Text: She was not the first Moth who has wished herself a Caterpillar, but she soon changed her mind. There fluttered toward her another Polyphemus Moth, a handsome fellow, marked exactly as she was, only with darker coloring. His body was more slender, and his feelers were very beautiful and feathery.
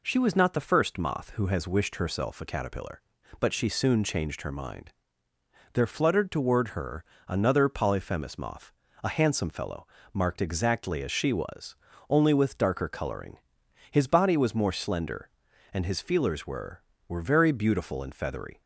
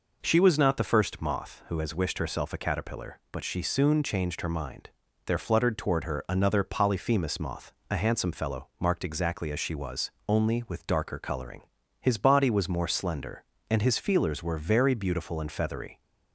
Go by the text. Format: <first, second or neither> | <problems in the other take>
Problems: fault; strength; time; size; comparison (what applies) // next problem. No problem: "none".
second | pauses between "her" and "another"; slight; at 7.0 s; 0.22 s long // says "were" twice; at 17.0 s